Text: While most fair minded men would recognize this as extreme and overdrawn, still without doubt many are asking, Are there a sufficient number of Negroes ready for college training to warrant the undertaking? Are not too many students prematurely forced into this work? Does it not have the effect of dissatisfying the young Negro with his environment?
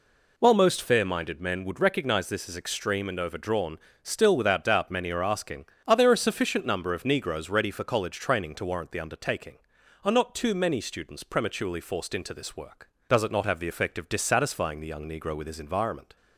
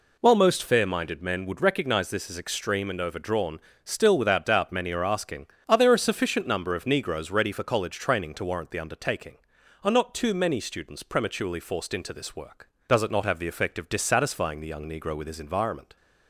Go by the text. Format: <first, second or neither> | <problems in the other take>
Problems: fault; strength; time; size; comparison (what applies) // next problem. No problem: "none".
neither | none